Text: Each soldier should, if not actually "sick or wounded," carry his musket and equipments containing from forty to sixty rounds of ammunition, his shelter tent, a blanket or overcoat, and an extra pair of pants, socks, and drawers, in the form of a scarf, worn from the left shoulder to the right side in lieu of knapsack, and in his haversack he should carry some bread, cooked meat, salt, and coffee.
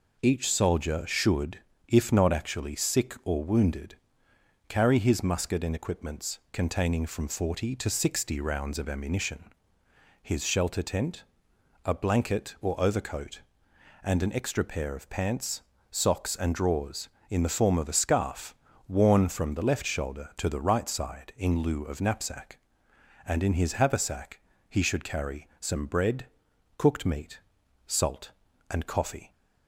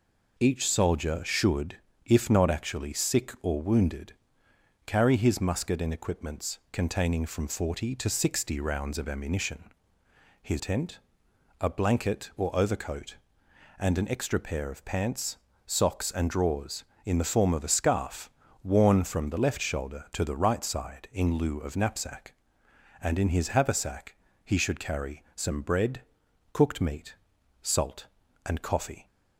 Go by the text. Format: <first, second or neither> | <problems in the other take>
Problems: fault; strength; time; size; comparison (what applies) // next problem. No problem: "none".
first | skips "shelter"; at 10.5 s // pauses between "haversack" and "he"; slight; at 24.1 s; 0.28 s long; slight in the first